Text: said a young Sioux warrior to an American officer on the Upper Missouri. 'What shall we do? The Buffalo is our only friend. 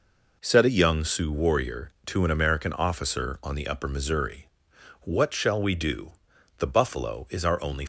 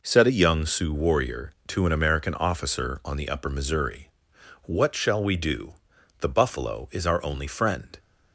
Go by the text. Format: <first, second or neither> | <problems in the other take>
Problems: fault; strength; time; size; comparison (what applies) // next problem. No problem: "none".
second | stops before "friend"; at 7.8 s